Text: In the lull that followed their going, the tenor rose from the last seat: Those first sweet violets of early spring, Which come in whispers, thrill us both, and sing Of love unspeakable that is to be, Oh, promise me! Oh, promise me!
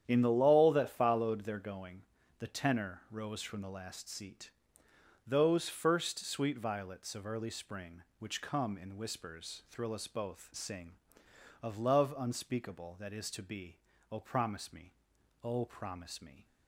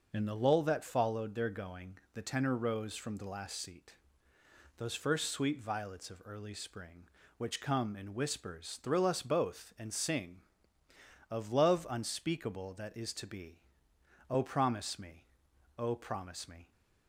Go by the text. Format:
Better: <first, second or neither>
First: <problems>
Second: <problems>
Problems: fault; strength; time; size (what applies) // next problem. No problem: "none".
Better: second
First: starts louder than the rest; strong; until 1.0 s; 9.5 dB // skips "and"; at 10.5 s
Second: none